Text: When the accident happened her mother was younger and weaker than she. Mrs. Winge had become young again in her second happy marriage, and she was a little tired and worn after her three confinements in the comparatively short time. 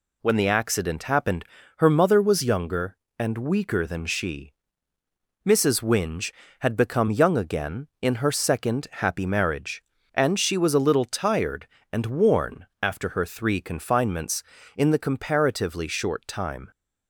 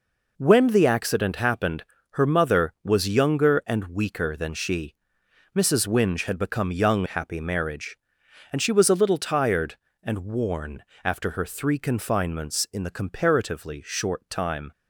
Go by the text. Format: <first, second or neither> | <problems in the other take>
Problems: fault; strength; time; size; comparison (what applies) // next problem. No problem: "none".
first | pauses between "happened" and "her"; slight; at 1.8 s; 0.26 s long; slight in the first // skips "again in her second"; at 7.0 s // pauses between "worn" and "after"; slight; at 10.8 s; 0.22 s long; slight in the first